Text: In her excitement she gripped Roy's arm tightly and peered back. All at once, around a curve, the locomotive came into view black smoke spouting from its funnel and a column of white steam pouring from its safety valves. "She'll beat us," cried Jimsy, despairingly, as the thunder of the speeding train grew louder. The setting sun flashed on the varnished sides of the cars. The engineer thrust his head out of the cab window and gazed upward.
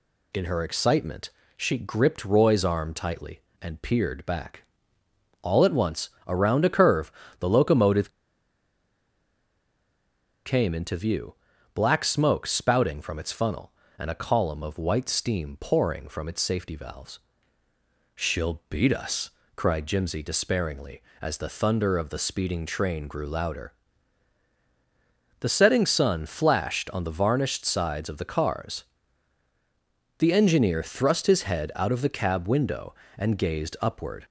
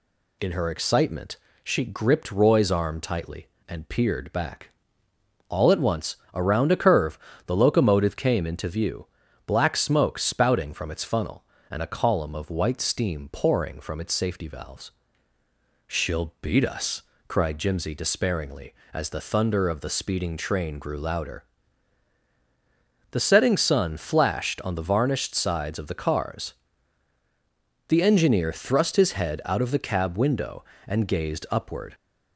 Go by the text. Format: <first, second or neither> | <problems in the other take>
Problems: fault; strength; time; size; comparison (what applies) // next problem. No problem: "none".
second | pauses between "excitement" and "she"; slight; at 1.3 s; 0.26 s long; slight in the second // pauses between "locomotive" and "came"; strong; at 8.0 s; 2.3 s long // pauses between "view" and "black"; at 11.3 s; 0.40 s long; also in the second